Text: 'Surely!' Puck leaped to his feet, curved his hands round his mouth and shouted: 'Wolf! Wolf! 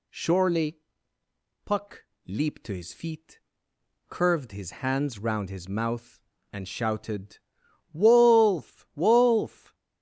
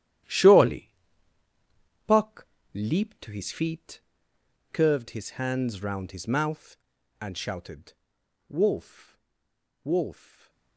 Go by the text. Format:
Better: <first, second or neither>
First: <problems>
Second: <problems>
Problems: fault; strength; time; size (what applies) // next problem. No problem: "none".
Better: first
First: pauses between "Puck" and "leaped"; slight; at 2.0 s; 0.18 s long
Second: gets quieter; strong; throughout; 11.5 dB // pauses between "Puck" and "leaped"; slight; at 2.4 s; 0.28 s long // stays silent after the last word; slight; from 10.1 s on; 0.6 s long